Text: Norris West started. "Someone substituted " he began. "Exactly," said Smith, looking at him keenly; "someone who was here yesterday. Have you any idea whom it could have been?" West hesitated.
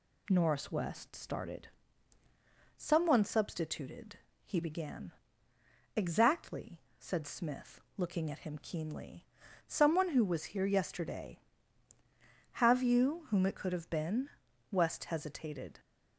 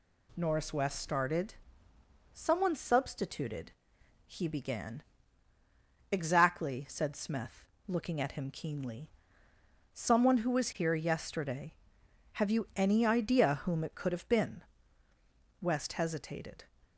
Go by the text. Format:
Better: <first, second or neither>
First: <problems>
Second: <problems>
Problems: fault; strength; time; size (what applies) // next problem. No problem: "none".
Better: second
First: skips "any idea"; at 13.2 s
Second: none